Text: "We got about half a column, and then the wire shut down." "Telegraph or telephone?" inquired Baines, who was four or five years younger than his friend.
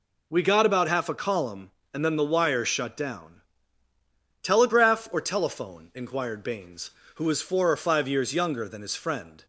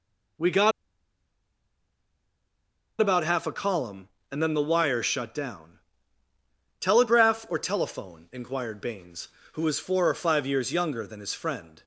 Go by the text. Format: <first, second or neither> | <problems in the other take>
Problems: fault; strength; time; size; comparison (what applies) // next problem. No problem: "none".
first | pauses between "got" and "about"; strong; at 0.7 s; 2.2 s long